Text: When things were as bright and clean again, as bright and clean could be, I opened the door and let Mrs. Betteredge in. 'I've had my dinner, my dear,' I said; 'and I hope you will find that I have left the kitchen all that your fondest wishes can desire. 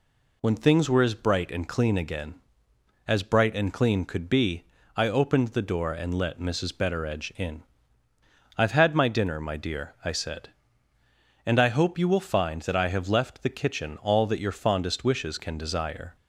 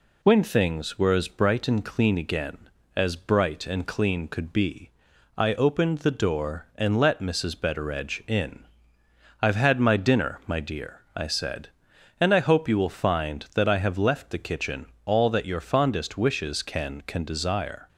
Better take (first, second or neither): first